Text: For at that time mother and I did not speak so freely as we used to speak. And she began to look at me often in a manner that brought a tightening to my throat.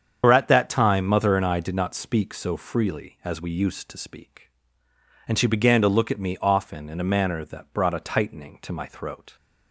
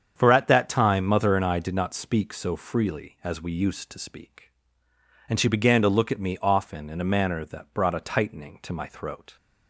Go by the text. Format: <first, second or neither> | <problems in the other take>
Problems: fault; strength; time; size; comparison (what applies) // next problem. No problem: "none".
second | loses the start of "For"; at 0.2 s; 65 ms // starts louder than the rest; strong; until 1.2 s; 7.5 dB; strong in the second